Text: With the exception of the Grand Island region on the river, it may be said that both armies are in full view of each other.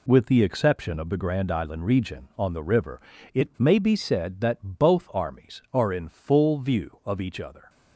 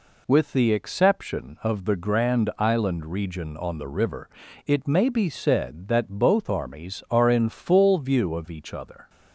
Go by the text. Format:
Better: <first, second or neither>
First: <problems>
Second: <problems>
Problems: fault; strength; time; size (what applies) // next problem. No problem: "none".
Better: neither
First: none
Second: none